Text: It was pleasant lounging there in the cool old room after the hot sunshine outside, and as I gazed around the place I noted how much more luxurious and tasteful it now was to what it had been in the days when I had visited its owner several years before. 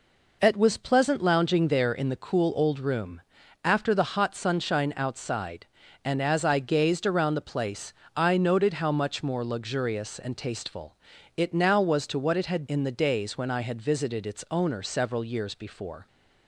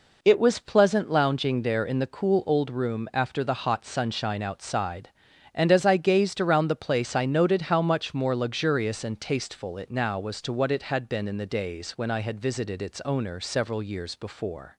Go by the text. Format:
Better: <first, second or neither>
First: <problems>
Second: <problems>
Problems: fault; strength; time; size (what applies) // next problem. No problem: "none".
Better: second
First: pauses between "room" and "after"; noticeable; at 3.1 s; 0.46 s long // pauses between "place" and "I"; slight; at 7.9 s; 0.24 s long // pauses between "tasteful" and "it"; at 10.9 s; 0.40 s long // skips "been"; at 12.6 s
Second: none